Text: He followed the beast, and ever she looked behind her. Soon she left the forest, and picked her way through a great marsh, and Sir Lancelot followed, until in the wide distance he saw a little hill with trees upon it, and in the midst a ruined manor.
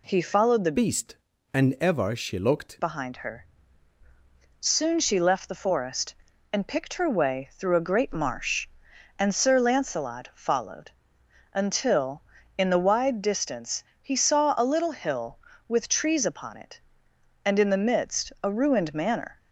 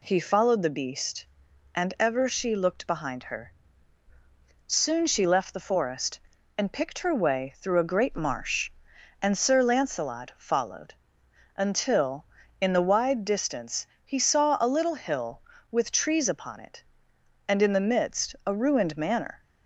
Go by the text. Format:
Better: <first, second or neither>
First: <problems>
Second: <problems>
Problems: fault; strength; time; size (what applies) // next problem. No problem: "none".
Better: second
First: changes voice from "beast" to "looked"; from 0.7 to 2.8 s; 2.1 s long // pauses between "distance" and "he"; slight; at 13.8 s; 0.20 s long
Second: pauses between "distance" and "he"; slight; at 13.8 s; 0.20 s long